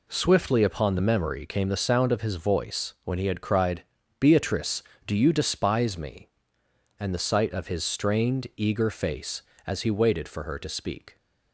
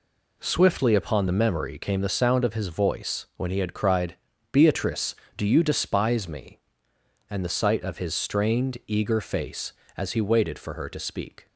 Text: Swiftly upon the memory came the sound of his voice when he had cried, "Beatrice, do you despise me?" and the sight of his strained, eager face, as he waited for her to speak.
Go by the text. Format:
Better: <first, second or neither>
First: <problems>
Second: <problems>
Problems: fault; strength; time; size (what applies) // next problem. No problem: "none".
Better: neither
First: none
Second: none